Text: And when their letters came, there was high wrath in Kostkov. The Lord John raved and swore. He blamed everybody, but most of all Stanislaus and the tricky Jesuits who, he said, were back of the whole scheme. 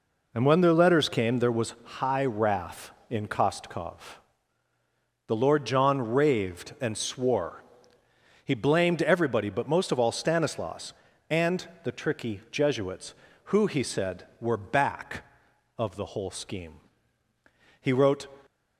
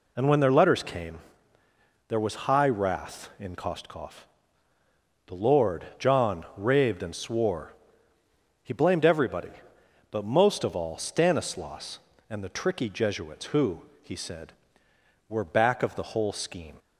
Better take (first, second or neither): second